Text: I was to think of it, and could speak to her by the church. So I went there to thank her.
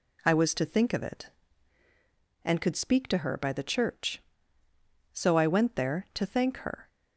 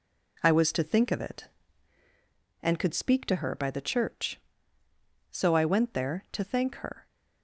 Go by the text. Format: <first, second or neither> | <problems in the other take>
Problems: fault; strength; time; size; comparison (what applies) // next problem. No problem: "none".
first | gets quieter; noticeable; throughout; 5 dB